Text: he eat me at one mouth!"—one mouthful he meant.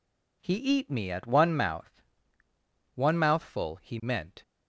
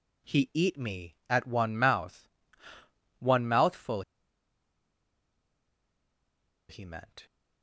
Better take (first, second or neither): first